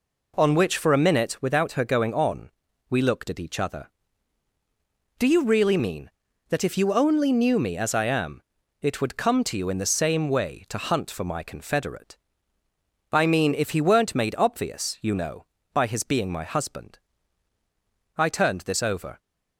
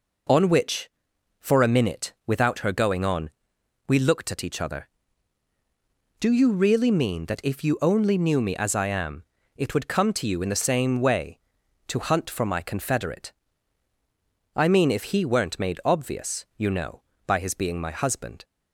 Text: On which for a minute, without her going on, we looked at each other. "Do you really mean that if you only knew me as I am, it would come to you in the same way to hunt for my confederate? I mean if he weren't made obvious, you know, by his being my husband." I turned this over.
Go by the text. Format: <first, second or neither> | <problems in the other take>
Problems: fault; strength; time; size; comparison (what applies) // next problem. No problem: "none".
first | stops before "I turned this over"; at 18.4 s